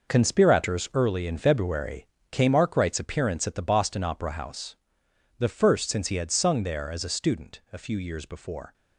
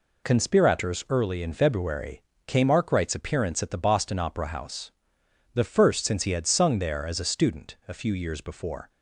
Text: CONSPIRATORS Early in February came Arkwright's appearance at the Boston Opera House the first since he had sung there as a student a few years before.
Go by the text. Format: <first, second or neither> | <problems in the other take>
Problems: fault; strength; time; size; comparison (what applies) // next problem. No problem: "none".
second | gets quieter; strong; throughout; 10 dB // pauses between "February" and "came"; slight; at 2.0 s; 0.24 s long; slight in the second // pauses between "House" and "the"; noticeable; at 4.7 s; 0.62 s long; noticeable in the second